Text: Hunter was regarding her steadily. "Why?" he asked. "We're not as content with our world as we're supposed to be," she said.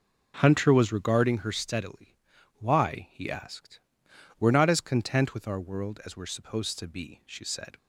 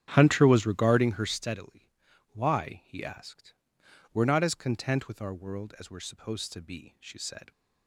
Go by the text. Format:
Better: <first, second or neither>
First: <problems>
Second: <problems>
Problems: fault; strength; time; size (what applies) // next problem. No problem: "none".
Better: first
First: none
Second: starts louder than the rest; strong; until 1.5 s; 9.5 dB